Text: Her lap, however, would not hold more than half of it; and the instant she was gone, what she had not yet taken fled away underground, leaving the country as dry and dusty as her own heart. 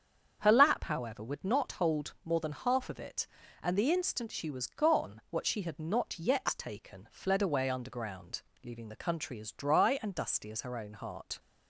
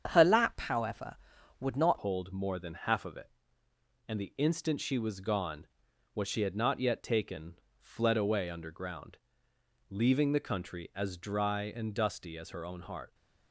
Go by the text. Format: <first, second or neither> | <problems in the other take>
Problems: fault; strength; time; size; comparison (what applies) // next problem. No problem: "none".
first | starts louder than the rest; strong; until 1.1 s; 8 dB; strong in the first // changes voice at "hold"; from 1.9 s on; 11.2 s long // pauses between "taken" and "fled"; slight; at 7.6 s; 0.18 s long